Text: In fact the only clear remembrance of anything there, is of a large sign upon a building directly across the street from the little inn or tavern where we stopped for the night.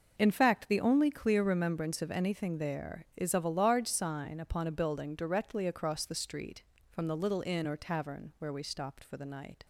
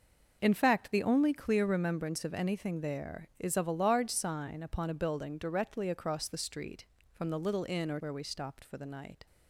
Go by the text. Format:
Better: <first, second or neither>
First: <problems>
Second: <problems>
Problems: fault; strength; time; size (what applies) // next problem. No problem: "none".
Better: first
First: none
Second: skips "tavern"; at 7.9 s